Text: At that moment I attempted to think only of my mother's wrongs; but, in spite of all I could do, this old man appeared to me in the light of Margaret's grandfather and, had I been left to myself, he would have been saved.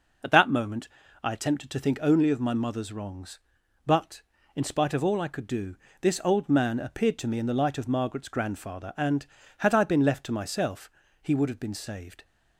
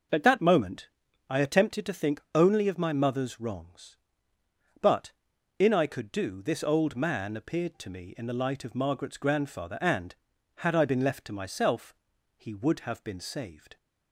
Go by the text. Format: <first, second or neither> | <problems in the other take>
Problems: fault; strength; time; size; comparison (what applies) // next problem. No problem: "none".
first | pauses between "moment" and "I"; at 0.8 s; 0.40 s long; slight in the first // skips "spite of all"; at 5.7 s